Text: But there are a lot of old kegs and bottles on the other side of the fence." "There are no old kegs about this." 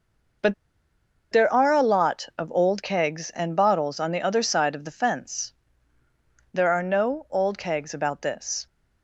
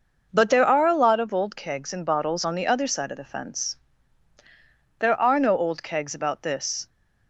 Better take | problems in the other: second | pauses between "But" and "there"; noticeable; at 0.5 s; 0.77 s long

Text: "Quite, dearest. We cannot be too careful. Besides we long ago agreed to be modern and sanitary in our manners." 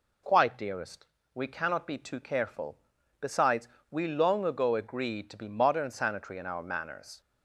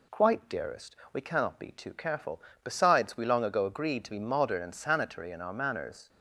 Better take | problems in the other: second | pauses between "Besides" and "we"; slight; at 3.6 s; 0.22 s long // skips "and"; at 5.9 s

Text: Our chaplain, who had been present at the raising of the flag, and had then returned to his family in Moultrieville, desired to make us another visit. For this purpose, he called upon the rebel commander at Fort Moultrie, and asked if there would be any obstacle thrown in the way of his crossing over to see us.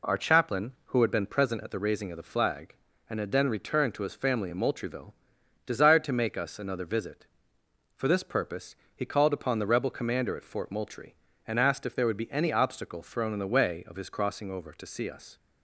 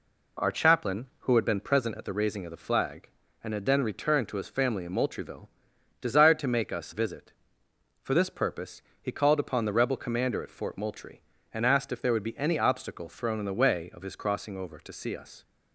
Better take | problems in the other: first | skips "another"; at 6.9 s

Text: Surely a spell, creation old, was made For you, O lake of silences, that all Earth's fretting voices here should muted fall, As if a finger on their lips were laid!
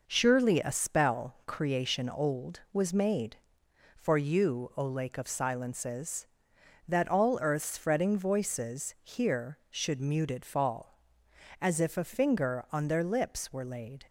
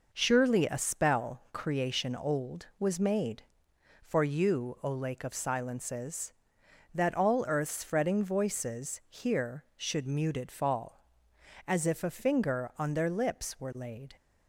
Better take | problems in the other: neither | none

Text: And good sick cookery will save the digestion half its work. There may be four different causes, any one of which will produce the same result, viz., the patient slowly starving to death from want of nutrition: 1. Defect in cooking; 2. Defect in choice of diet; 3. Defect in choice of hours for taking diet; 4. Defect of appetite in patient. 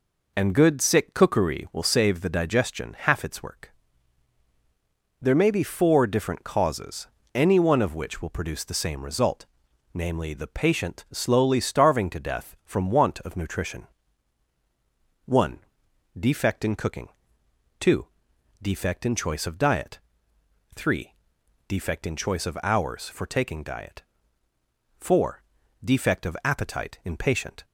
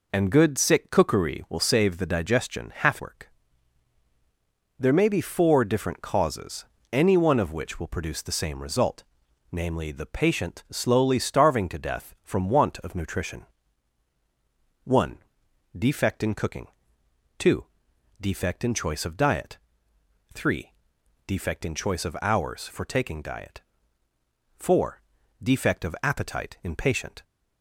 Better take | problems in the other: first | skips "its"; at 3.0 s

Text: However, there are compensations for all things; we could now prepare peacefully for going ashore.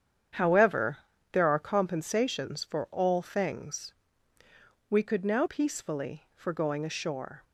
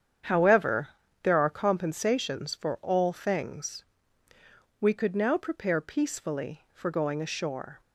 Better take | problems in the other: second | starts louder than the rest; strong; until 1.7 s; 8.5 dB; strong in the second // skips "prepare"; at 5.4 s

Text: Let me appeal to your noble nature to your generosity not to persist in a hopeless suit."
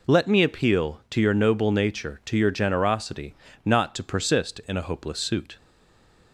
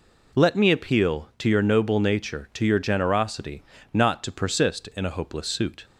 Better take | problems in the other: second | pauses between "generosity" and "not"; slight; at 3.3 s; 0.32 s long; slight in the second // stays silent after the last word; slight; from 5.5 s on; 0.8 s long

